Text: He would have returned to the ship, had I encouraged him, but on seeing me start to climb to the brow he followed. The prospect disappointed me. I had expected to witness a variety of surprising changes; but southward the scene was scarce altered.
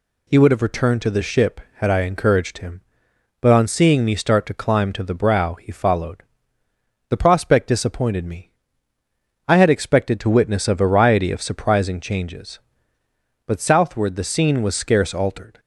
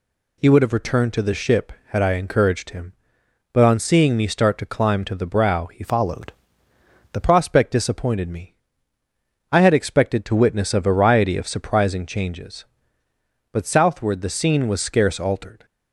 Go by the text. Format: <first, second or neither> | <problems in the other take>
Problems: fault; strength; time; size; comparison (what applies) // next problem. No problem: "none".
first | changes voice from "followed" to "The"; from 5.8 to 7.2 s; 1.4 s long